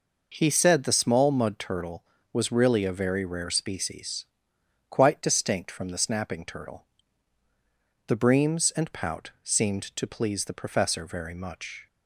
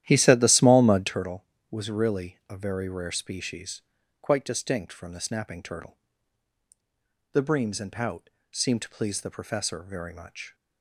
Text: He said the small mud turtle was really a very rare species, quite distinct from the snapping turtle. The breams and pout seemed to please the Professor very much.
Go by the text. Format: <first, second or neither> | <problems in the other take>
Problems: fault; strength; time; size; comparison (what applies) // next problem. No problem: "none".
first | starts louder than the rest; strong; until 1.3 s; 12 dB // pauses between "pout" and "seemed"; slight; at 8.2 s; 0.22 s long